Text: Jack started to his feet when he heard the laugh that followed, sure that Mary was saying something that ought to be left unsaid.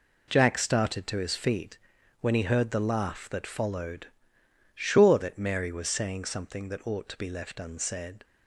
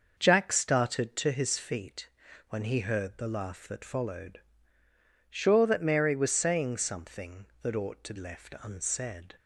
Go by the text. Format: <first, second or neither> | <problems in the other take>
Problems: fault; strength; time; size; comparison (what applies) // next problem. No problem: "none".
first | pauses between "feet" and "when"; at 2.0 s; 0.40 s long; also in the first // skips "be"; at 8.1 s